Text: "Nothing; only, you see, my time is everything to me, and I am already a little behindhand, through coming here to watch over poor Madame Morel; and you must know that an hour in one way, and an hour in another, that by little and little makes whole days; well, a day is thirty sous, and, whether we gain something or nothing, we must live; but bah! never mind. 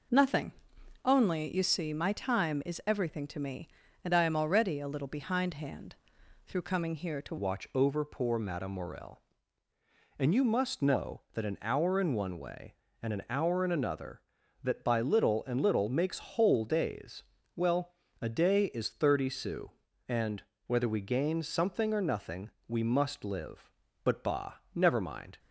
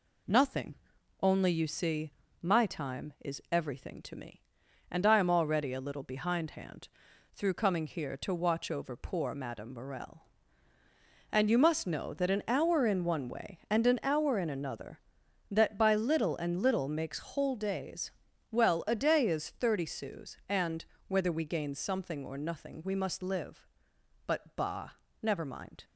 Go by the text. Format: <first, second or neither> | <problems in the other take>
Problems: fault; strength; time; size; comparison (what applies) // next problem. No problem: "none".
second | changes voice at "watch"; from 7.3 s on; 18.0 s long